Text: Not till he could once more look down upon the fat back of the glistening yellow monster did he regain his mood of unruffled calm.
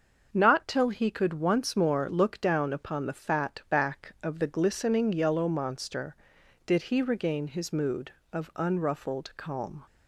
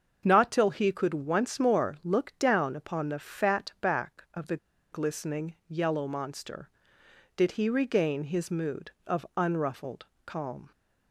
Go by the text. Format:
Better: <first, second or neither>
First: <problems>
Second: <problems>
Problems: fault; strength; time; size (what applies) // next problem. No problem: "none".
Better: first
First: starts louder than the rest; until 1.3 s; 6.5 dB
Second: starts louder than the rest; until 1.2 s; 7 dB // pauses between "the" and "glistening"; slight; at 4.5 s; 0.36 s long // pauses between "unruffled" and "calm"; slight; at 10.0 s; 0.18 s long